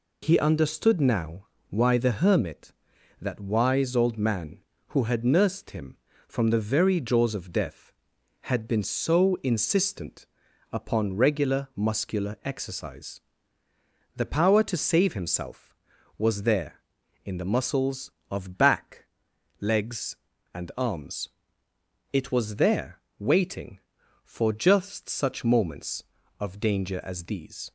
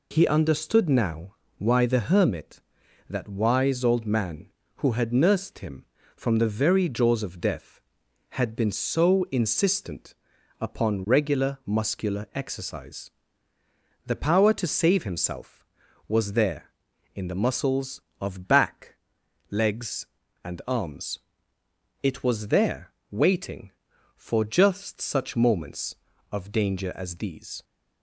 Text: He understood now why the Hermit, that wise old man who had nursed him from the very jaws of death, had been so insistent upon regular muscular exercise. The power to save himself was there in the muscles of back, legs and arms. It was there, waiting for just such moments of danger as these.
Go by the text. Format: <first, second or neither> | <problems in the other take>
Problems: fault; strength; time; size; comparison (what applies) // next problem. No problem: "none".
neither | pauses between "now" and "why"; slight; the same in both // pauses between "insistent" and "upon"; noticeable; the same in both